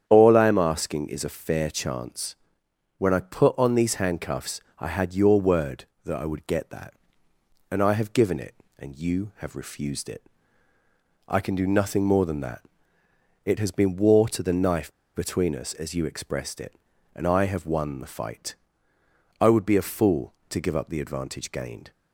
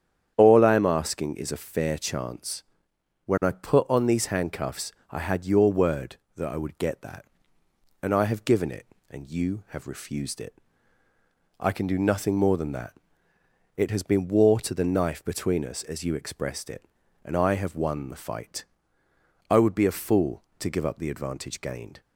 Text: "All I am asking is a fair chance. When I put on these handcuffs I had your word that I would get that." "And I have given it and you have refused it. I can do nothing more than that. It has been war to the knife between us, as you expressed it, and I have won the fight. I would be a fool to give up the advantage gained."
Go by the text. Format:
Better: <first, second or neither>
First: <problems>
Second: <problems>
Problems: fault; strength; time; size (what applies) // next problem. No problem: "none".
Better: second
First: starts louder than the rest; strong; until 1.0 s; 9 dB // pauses between "handcuffs" and "I"; slight; at 4.6 s; 0.18 s long // pauses between "knife" and "between"; slight; at 14.9 s; 0.22 s long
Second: starts louder than the rest; strong; until 1.3 s; 9 dB // pauses between "handcuffs" and "I"; slight; at 4.9 s; 0.18 s long